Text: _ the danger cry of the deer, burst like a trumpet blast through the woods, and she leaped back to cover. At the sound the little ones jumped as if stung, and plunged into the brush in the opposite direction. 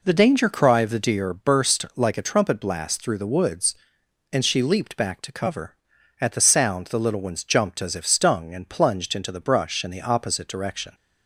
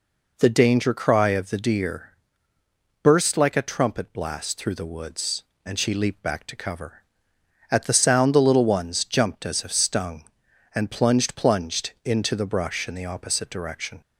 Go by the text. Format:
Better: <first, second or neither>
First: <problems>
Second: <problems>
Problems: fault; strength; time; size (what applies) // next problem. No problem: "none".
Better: first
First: none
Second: says "plunged" twice; at 11.3 s